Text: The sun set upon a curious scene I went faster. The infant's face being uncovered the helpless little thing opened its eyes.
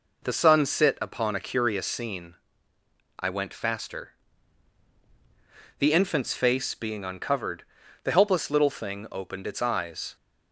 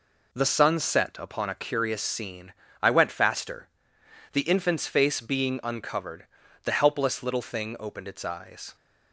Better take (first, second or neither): second